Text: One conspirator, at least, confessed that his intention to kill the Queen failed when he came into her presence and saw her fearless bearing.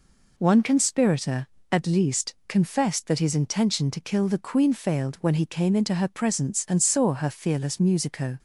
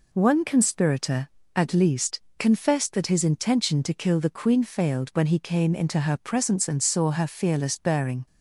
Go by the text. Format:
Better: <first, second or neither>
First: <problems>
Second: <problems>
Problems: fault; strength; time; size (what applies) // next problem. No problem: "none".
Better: second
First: says "musico" for "bearing"; at 7.7 s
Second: none